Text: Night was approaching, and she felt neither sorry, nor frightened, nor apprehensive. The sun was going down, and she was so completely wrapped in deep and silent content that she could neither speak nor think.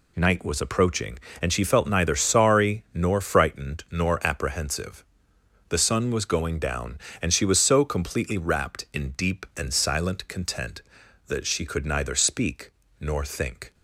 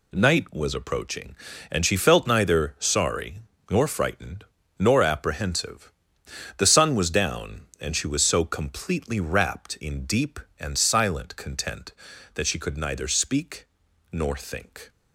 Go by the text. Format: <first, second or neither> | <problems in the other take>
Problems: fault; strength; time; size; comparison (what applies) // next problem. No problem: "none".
first | skips "going"; at 7.1 s // pauses between "speak" and "nor"; noticeable; at 13.6 s; 0.46 s long; slight in the first